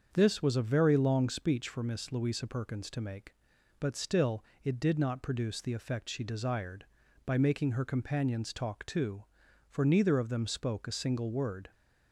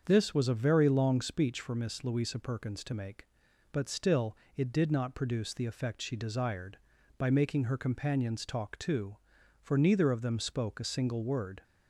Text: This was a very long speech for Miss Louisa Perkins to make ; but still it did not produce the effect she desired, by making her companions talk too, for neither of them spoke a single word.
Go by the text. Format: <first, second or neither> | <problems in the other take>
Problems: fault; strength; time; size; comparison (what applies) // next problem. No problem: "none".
neither | starts louder than the rest; the same in both // pauses between "still" and "it"; slight; the same in both